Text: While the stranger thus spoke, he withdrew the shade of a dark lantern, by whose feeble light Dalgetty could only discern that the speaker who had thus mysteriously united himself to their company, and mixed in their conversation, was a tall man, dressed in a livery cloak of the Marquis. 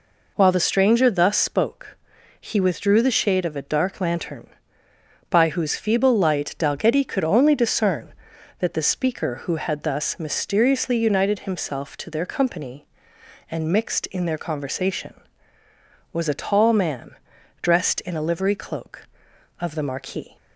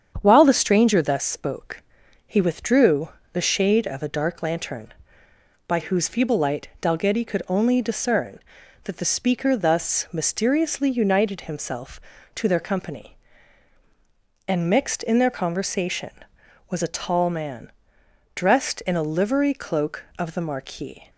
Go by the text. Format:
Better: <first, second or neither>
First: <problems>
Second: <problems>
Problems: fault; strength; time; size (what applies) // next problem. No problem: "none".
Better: first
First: none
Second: starts louder than the rest; strong; until 1.2 s; 8 dB // pauses between "withdrew" and "the"; slight; at 3.0 s; 0.24 s long // skips "who had"; at 9.5 s